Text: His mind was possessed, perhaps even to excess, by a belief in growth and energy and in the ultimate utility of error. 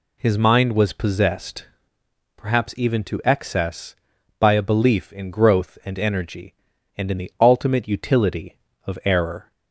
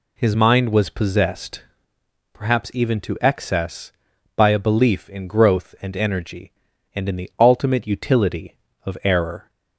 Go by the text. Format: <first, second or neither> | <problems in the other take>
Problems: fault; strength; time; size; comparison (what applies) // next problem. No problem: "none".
neither | none